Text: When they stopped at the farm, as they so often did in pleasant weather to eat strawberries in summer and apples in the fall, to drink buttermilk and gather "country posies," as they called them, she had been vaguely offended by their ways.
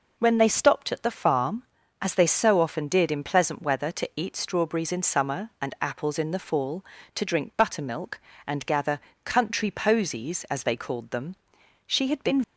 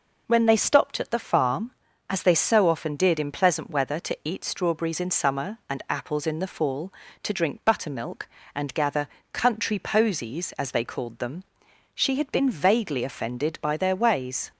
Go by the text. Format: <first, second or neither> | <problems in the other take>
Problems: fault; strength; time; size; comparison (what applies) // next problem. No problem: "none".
second | pauses between "gather" and "country"; slight; at 8.9 s; 0.26 s long; slight in the second // stops before "vaguely offended by their ways"; at 12.4 s